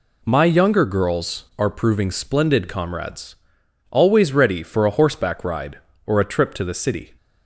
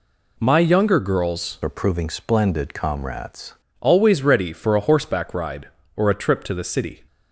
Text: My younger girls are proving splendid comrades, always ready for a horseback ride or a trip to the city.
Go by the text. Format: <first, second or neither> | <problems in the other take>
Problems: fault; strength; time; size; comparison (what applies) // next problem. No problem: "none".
first | changes voice from "are" to "comrades"; from 1.6 to 3.5 s; 1.9 s long